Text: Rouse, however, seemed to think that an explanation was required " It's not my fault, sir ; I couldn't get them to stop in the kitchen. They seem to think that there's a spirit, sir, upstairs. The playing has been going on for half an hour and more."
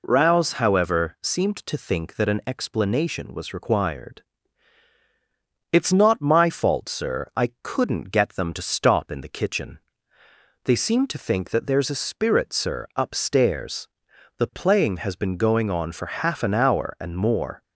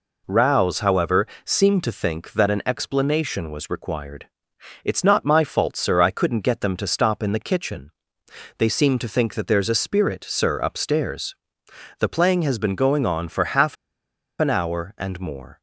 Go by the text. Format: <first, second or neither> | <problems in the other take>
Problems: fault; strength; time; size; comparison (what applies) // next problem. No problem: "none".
first | pauses between "half" and "an"; noticeable; at 13.7 s; 0.64 s long